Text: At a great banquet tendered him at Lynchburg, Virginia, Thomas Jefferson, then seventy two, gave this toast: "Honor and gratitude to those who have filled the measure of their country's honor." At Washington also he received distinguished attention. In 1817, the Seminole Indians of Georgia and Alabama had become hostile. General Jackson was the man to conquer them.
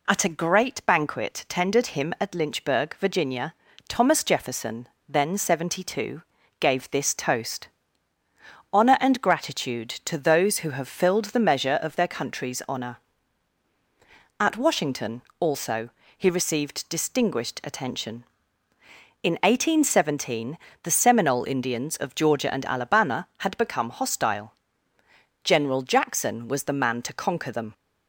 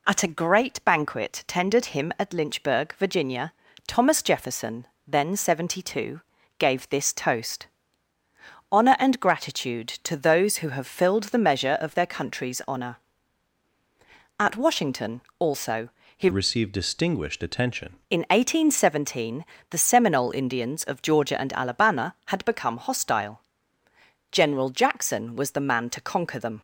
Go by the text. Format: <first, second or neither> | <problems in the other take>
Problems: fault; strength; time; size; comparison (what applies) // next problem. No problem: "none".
first | pauses between "Washington" and "also"; slight; at 15.2 s; 0.18 s long; slight in the first // pauses between "also" and "he"; slight; at 15.8 s; 0.26 s long; slight in the first // changes voice from "received" to "attention"; from 16.3 to 17.9 s; 1.6 s long